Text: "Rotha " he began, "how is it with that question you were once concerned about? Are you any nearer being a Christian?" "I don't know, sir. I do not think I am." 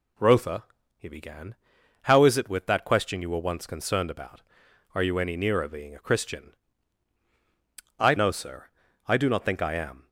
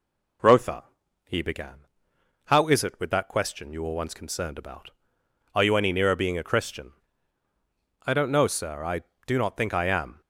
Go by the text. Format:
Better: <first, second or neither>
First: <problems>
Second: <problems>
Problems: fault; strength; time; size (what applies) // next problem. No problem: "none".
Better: second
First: skips "don't"; at 8.1 s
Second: none